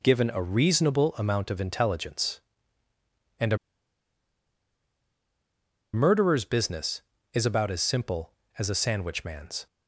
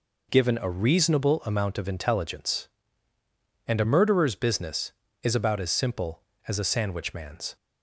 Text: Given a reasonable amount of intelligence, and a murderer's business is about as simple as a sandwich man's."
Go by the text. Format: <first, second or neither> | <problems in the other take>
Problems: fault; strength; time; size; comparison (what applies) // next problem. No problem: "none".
second | pauses between "a" and "murderer's"; strong; at 3.5 s; 2.3 s long